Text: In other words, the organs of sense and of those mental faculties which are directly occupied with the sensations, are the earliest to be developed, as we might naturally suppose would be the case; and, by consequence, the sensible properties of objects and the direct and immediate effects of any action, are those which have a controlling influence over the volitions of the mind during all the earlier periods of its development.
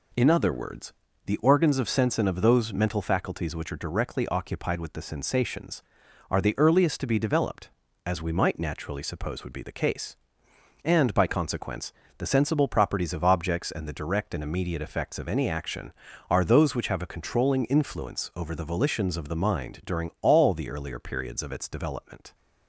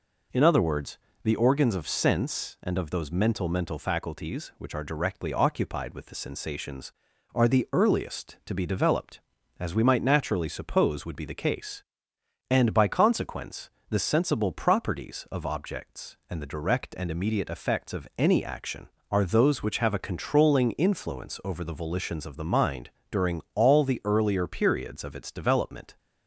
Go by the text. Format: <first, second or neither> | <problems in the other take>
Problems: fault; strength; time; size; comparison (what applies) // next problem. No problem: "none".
first | says "mental" twice; at 3.4 s // pauses between "mind" and "during"; slight; at 22.8 s; 0.22 s long